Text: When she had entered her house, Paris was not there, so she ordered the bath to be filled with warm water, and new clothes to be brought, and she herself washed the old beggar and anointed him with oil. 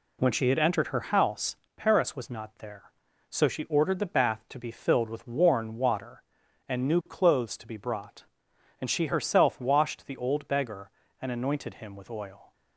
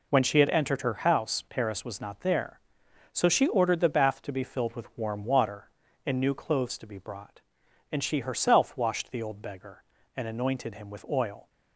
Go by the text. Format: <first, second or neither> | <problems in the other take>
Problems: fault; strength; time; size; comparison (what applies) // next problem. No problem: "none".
second | says "worn" for "warm"; at 5.2 s